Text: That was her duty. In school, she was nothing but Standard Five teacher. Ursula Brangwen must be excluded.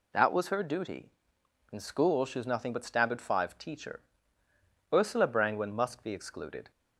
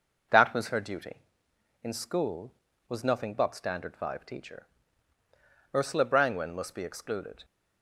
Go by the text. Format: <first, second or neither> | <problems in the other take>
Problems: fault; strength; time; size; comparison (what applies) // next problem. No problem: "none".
first | skips "she"; at 2.7 s